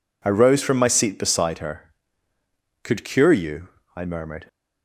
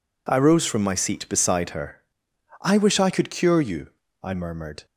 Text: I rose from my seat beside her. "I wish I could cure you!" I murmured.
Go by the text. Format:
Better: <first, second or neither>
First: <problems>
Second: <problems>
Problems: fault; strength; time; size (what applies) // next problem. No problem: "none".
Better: second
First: skips "I wish I"; at 2.3 s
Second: none